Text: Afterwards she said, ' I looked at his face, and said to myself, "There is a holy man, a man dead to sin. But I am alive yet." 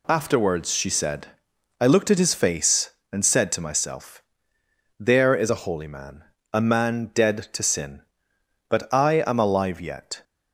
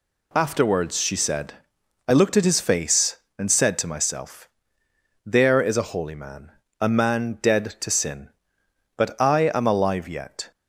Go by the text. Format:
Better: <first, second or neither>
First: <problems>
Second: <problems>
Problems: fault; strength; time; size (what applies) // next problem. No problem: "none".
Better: neither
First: none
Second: none